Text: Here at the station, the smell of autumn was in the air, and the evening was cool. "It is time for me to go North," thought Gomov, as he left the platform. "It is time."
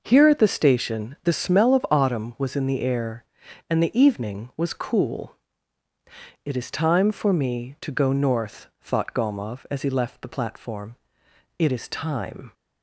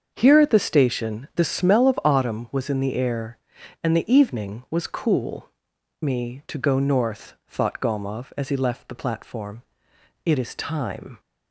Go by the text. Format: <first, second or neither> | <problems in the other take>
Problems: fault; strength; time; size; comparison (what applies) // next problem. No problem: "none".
first | starts louder than the rest; until 1.1 s; 6.5 dB // skips "It is time for"; at 5.7 s